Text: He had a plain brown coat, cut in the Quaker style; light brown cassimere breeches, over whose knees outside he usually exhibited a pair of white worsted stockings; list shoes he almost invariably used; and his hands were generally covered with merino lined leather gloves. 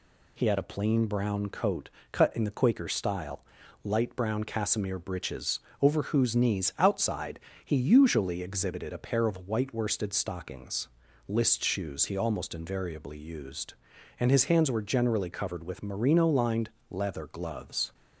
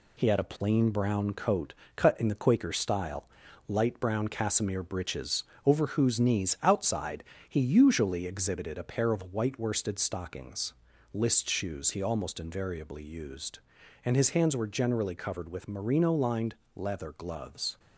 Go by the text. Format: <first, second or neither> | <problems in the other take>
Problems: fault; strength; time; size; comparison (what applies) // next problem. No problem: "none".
first | gets quieter; noticeable; throughout; 5 dB // pauses between "outside" and "he"; slight; at 7.2 s; 0.26 s long; slight in the first // pauses between "lined" and "leather"; slight; at 16.5 s; 0.22 s long; slight in the first